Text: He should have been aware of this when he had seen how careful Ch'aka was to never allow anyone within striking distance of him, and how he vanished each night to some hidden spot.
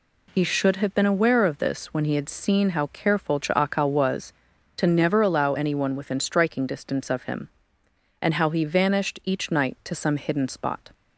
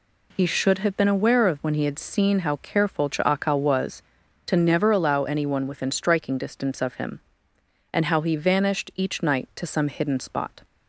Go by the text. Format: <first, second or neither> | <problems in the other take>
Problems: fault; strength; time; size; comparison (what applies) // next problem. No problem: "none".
first | skips "this"; at 1.5 s